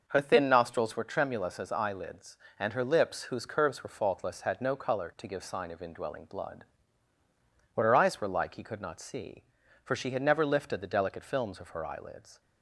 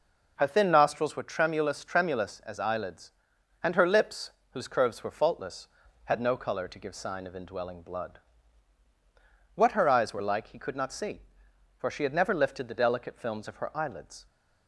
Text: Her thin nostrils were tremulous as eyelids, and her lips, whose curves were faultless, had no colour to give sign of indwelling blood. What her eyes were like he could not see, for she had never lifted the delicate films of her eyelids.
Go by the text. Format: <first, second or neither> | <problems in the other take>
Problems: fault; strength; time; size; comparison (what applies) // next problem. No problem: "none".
first | says "tremulous" twice; at 1.8 s